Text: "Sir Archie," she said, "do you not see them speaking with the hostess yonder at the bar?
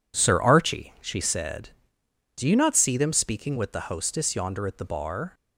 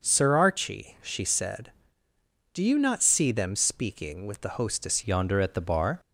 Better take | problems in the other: first | changes voice at "yonder"; from 5.0 s on; 0.9 s long

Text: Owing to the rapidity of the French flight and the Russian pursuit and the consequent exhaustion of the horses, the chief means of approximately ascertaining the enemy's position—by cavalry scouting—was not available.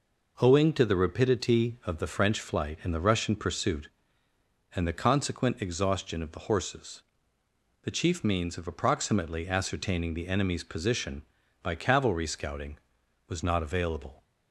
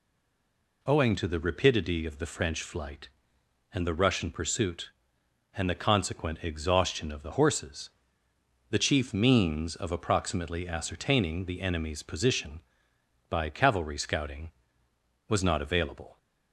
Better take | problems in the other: first | stays silent before the first word; slight; until 0.8 s; 0.8 s long

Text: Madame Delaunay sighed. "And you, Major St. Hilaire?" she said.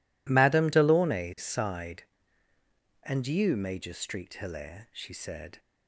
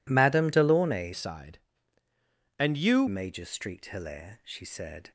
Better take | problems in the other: first | changes voice from "sighed" to "you"; from 1.1 to 3.0 s; 1.9 s long

